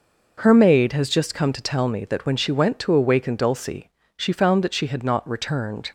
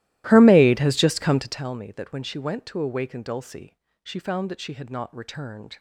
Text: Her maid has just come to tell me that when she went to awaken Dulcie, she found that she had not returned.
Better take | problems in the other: first | starts louder than the rest; strong; until 1.7 s; 15.5 dB

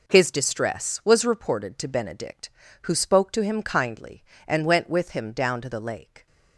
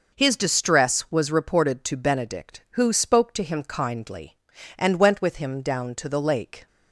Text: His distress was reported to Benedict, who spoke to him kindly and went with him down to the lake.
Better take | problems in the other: second | gets quieter; strong; throughout; 10 dB

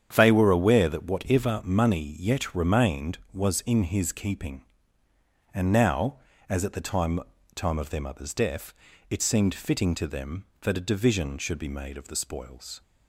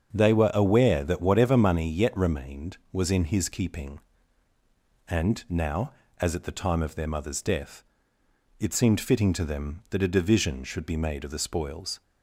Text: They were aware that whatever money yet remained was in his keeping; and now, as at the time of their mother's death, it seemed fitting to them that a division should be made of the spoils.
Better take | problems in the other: second | starts louder than the rest; strong; until 1.1 s; 8.5 dB; also in the second // says "time" twice; at 7.5 s

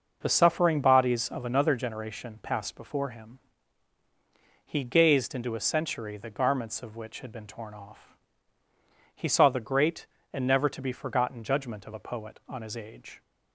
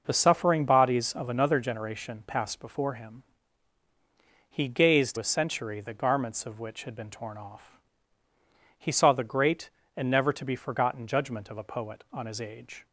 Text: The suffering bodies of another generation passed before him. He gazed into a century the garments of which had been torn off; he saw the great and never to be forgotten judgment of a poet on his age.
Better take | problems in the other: first | skips "into"; at 5.1 s

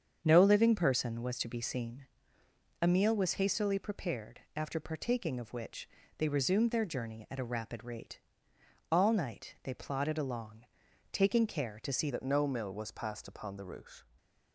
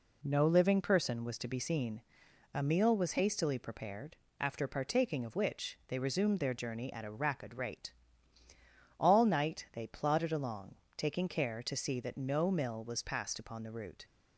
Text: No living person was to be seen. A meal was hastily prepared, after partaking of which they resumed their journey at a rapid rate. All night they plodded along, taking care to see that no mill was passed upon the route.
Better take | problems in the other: second | starts louder than the rest; strong; until 1.2 s; 7.5 dB // pauses between "which" and "they"; slight; at 5.8 s; 0.30 s long // changes voice at "that"; from 12.1 s on; 1.9 s long // stays silent after the last word; slight; from 14.0 s on; 0.5 s long

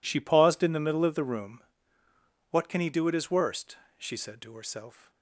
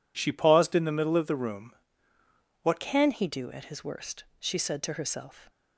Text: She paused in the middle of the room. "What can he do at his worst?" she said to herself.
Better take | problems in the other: first | changes voice at "can"; from 2.7 s on; 2.7 s long

